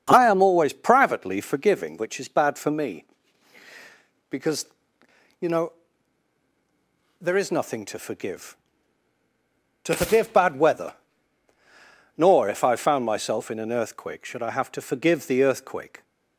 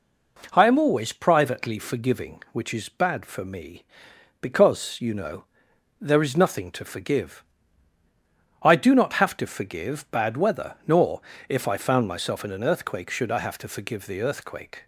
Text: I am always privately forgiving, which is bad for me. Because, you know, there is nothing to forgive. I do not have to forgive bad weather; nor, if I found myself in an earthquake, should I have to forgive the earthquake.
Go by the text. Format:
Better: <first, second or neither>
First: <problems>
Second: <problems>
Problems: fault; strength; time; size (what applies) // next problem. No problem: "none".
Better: second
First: starts louder than the rest; strong; until 1.0 s; 7 dB // skips "I do not have"; at 9.2 s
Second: none